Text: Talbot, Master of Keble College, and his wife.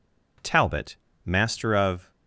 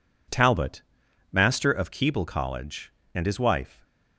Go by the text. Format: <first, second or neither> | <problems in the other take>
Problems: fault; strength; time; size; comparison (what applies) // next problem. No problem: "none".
second | stops before "Keble College and his wife"; at 2.1 s